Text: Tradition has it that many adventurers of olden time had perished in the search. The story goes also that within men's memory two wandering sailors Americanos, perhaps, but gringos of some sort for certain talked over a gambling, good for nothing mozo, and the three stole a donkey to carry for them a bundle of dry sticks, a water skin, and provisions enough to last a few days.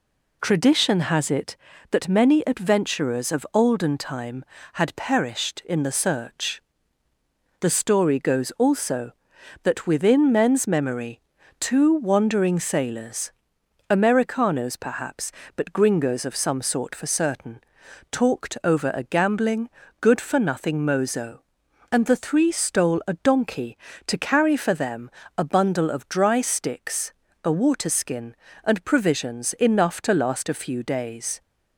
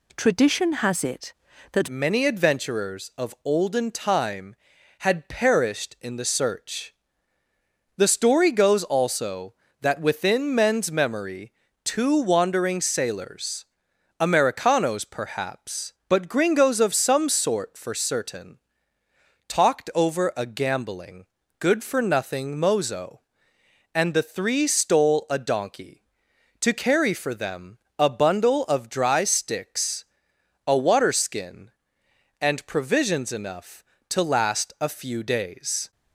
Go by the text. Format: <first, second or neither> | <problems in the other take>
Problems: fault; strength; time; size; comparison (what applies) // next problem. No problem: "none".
first | changes voice at "many"; from 1.8 s on; 34.1 s long // pauses between "memory" and "two"; slight; at 11.5 s; 0.32 s long; also in the first // pauses between "sailors" and "Americanos"; noticeable; at 13.6 s; 0.54 s long; noticeable in the first // pauses between "certain" and "talked"; noticeable; at 18.5 s; 0.90 s long; noticeable in the first // pauses between "them" and "a"; slight; at 27.7 s; 0.22 s long; slight in the first